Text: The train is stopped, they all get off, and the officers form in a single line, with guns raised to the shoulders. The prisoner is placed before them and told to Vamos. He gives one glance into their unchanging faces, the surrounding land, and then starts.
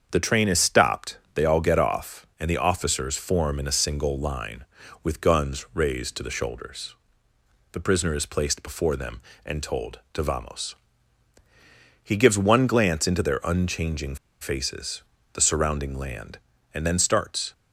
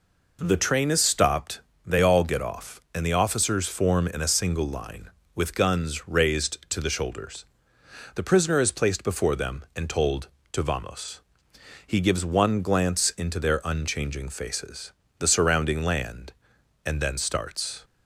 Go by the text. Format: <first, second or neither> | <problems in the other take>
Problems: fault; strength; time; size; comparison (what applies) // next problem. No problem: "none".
second | starts louder than the rest; strong; until 1.1 s; 7 dB // pauses between "unchanging" and "faces"; slight; at 14.1 s; 0.25 s long